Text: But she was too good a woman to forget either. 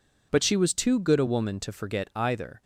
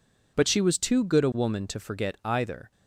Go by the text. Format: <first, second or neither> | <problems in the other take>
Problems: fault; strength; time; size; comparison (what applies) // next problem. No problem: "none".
neither | none